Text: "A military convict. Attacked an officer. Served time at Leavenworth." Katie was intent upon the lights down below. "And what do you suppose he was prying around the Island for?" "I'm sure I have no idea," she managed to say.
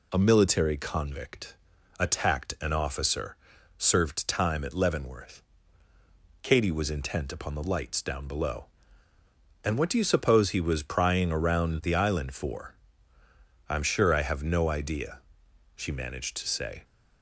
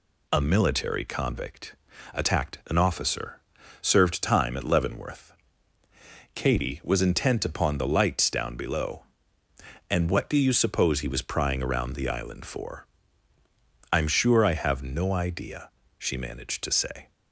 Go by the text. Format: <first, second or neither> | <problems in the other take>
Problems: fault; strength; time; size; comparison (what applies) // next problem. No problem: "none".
neither | none